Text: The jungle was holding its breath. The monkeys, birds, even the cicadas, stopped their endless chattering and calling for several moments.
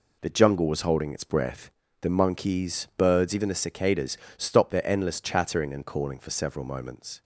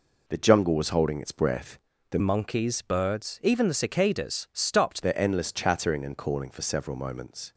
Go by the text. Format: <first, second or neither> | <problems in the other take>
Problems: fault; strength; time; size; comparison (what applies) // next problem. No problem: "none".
first | changes voice from "monkeys" to "stopped"; from 2.1 to 5.0 s; 2.9 s long